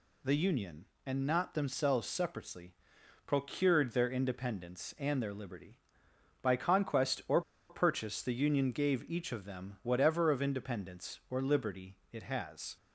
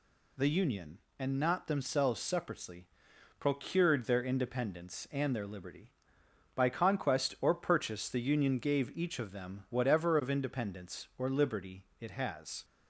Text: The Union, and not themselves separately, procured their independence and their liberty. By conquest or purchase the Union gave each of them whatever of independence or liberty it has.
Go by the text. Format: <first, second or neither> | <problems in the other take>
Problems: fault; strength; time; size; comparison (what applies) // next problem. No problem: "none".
second | pauses between "or" and "purchase"; slight; at 7.4 s; 0.27 s long // pauses between "liberty" and "it"; slight; at 11.9 s; 0.16 s long; slight in the second